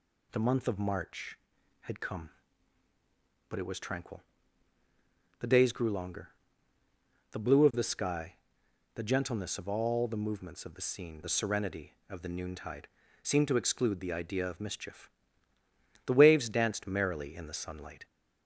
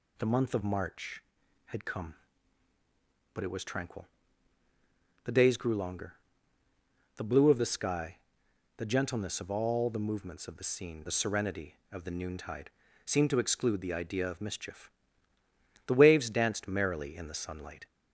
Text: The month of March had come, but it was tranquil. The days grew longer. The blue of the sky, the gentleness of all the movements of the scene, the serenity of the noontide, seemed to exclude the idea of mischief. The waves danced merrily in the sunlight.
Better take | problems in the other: neither | none

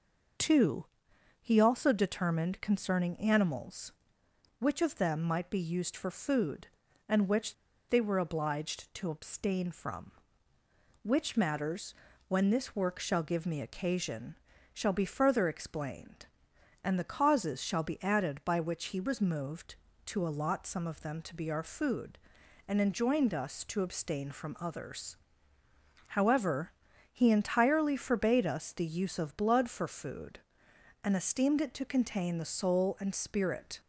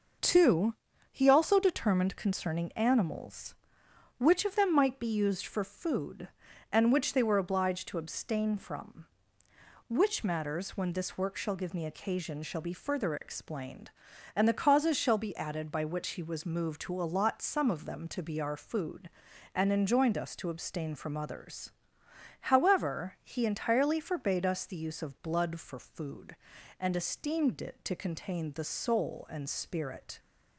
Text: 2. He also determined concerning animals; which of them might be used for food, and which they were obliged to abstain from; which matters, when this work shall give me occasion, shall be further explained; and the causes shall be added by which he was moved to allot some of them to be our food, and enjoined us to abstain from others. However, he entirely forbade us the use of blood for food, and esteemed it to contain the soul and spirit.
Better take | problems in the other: second | pauses between "which" and "they"; slight; at 7.5 s; 0.34 s long

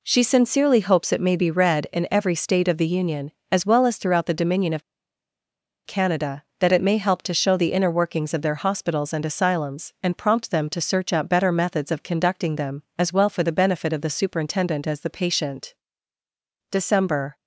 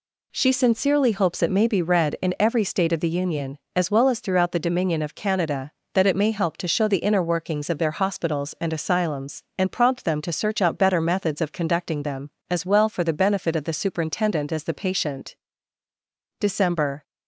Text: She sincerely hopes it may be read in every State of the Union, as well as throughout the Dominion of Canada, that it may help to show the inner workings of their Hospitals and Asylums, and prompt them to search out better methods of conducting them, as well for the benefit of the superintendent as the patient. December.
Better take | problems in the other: second | pauses between "of" and "Canada"; at 4.8 s; 1.0 s long

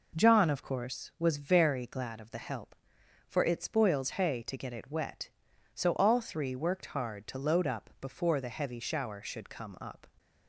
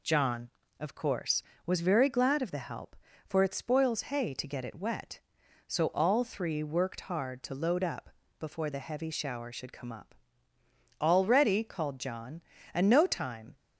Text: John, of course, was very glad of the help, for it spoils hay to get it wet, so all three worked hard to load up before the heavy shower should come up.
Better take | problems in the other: first | pauses between "up" and "before"; slight; at 8.0 s; 0.28 s long // goes on to say "All ready called John and no time"; strong; from 10.9 s on; 2.5 s long

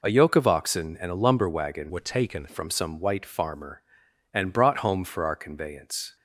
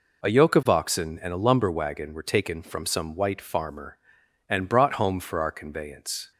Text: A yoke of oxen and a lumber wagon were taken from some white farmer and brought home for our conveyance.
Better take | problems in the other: second | changes voice from "were" to "taken"; from 1.8 to 2.4 s; 0.6 s long

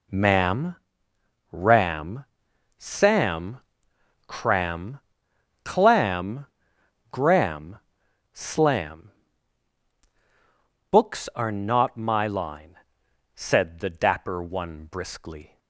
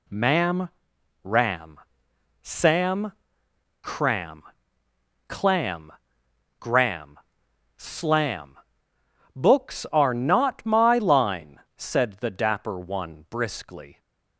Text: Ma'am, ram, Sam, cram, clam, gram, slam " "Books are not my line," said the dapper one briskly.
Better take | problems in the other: neither | none

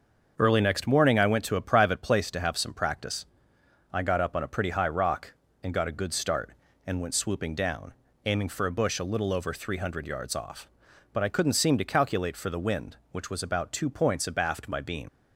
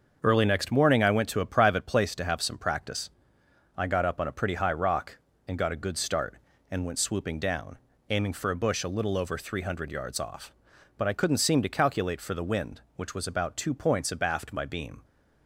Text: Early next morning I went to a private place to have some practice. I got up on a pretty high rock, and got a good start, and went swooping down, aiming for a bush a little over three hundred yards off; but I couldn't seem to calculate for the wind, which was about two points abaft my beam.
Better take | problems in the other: second | starts louder than the rest; until 1.3 s; 6.5 dB; also in the second // leaves "beam" unfinished; at 15.0 s; 105 ms

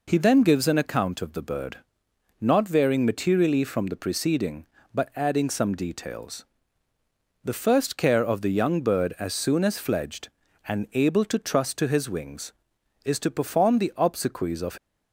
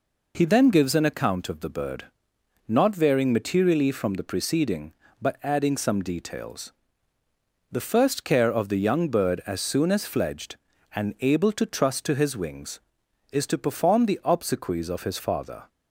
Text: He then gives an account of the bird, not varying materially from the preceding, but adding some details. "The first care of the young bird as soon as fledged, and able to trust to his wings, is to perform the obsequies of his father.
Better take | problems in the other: second | stops before "his father"; at 14.7 s

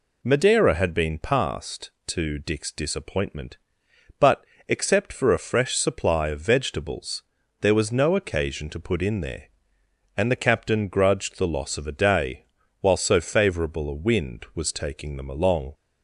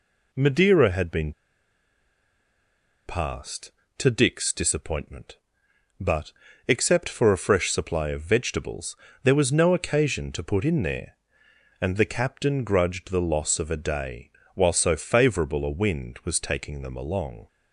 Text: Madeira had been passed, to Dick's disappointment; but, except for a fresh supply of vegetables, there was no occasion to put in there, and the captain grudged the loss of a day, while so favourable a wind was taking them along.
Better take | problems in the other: first | pauses between "been" and "passed"; strong; at 1.3 s; 1.7 s long

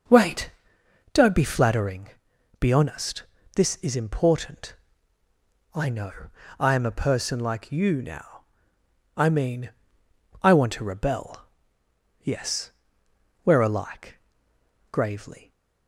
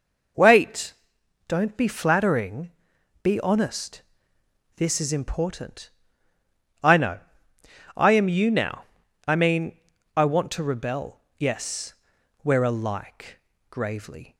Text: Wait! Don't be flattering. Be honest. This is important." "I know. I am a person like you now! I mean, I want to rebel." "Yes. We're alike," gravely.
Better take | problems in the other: first | skips "a person like"; at 8.2 s

